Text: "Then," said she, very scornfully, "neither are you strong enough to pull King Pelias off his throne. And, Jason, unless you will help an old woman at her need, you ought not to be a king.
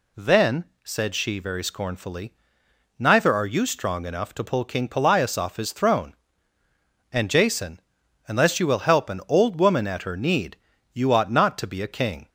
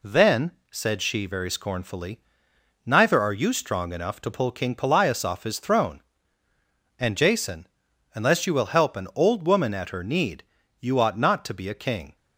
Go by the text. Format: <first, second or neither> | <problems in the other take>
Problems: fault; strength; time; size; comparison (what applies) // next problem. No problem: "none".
first | gets quieter; slight; throughout; 2.5 dB